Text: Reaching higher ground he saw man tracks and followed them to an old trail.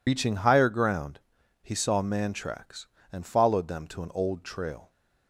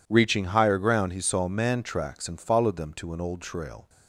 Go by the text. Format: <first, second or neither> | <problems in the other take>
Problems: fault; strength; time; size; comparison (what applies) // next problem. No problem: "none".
second | loses the start of "Reaching"; at 0.0 s; 80 ms // pauses between "ground" and "he"; at 1.1 s; 0.44 s long